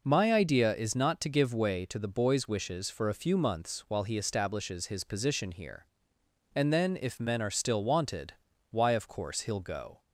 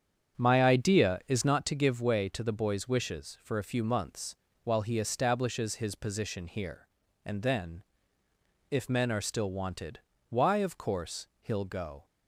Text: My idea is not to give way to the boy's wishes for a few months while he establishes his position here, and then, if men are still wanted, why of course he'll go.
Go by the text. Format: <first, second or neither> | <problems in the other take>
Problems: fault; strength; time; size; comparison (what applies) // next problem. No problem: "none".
first | starts louder than the rest; strong; until 1.7 s; 8 dB // pauses between "months" and "while"; slight; at 4.3 s; 0.30 s long